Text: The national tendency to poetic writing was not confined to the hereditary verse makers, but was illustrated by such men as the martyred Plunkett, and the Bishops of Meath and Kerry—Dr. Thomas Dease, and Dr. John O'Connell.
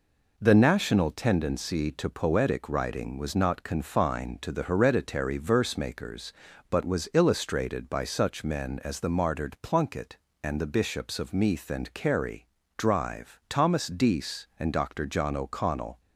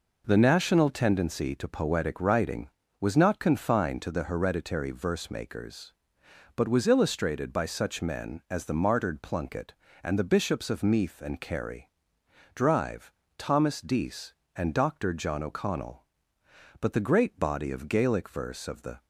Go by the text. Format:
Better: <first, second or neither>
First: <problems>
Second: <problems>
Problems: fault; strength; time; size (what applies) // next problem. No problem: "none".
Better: first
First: none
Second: goes on to say "But the great body of Gaelic verse of the"; strong; from 16.7 s on; 2.2 s long